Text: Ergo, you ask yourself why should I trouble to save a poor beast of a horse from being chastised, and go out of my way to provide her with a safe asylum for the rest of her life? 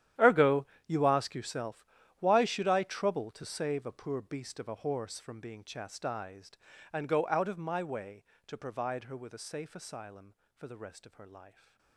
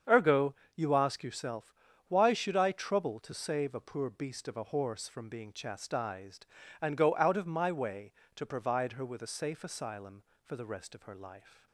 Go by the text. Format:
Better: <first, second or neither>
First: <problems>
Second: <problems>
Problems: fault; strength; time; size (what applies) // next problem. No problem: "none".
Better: second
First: gets quieter; strong; throughout; 18.5 dB // starts louder than the rest; strong; until 1.4 s; 11 dB // pauses between "yourself" and "why"; slight; at 1.8 s; 0.36 s long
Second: starts louder than the rest; strong; until 1.2 s; 7.5 dB // pauses between "yourself" and "why"; slight; at 1.7 s; 0.36 s long